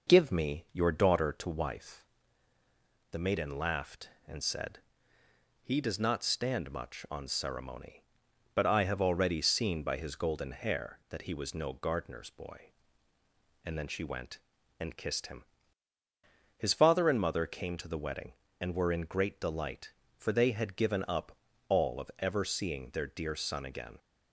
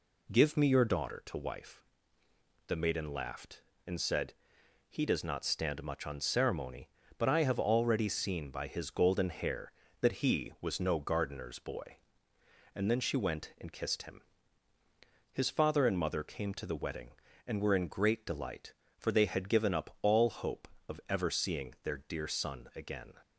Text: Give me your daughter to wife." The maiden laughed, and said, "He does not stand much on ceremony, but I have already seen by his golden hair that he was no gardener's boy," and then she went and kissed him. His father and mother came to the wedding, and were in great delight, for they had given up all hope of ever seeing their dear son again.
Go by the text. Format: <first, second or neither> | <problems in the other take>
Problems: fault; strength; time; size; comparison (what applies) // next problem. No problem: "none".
second | pauses between "up" and "all"; slight; at 21.3 s; 0.32 s long // skips "hope"; at 22.0 s